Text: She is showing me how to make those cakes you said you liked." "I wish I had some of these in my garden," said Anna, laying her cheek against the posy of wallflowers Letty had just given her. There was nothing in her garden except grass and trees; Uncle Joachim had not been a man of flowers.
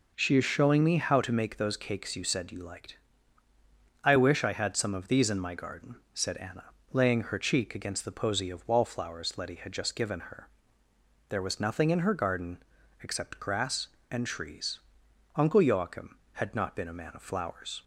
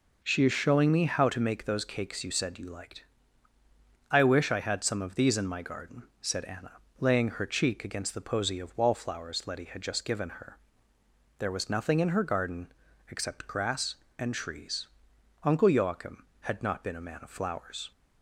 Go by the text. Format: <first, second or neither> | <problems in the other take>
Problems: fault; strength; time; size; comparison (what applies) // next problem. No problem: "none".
neither | pauses between "garden" and "except"; the same in both